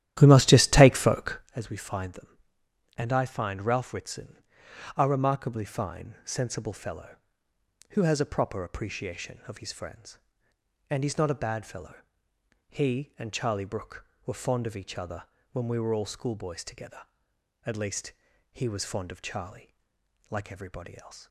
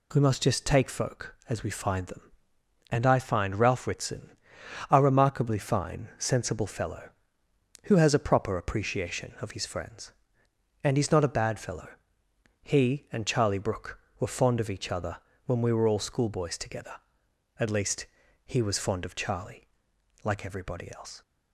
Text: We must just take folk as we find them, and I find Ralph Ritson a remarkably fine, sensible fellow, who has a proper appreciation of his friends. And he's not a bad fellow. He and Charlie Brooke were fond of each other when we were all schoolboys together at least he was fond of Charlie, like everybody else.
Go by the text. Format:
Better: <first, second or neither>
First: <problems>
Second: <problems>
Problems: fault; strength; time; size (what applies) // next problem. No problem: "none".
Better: second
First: starts louder than the rest; strong; until 1.6 s; 12.5 dB // pauses between "Ritson" and "a"; noticeable; at 4.3 s; 0.58 s long // pauses between "other" and "when"; slight; at 15.2 s; 0.28 s long // pauses between "least" and "he"; at 18.1 s; 0.38 s long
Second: pauses between "Ritson" and "a"; noticeable; at 4.3 s; 0.58 s long // pauses between "other" and "when"; slight; at 15.1 s; 0.28 s long // pauses between "least" and "he"; at 18.0 s; 0.38 s long